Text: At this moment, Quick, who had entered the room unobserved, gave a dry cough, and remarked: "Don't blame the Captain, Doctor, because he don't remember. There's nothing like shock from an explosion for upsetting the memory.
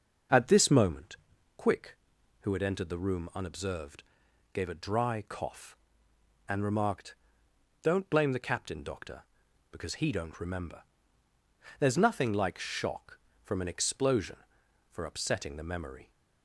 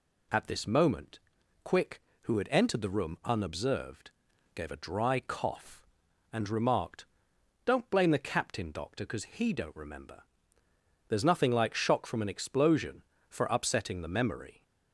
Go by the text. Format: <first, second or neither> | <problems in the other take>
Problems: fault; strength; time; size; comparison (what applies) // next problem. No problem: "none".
second | starts louder than the rest; until 1.4 s; 6 dB